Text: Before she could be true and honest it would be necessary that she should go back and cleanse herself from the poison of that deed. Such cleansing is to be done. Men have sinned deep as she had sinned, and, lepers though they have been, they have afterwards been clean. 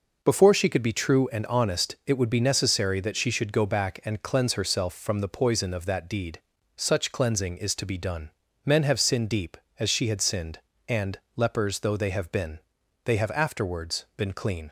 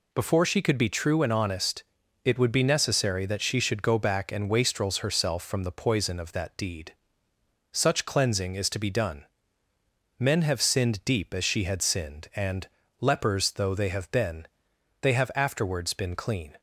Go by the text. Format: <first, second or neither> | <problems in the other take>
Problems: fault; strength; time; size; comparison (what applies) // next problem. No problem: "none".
first | pauses between "honest" and "it"; at 1.8 s; 0.40 s long // says "wastrels" for "cleanse"; at 4.4 s